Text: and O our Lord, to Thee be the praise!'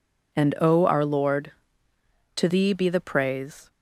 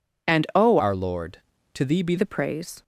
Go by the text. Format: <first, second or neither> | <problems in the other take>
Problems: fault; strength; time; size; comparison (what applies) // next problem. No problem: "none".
first | changes voice from "our" to "be"; from 0.7 to 2.1 s; 1.4 s long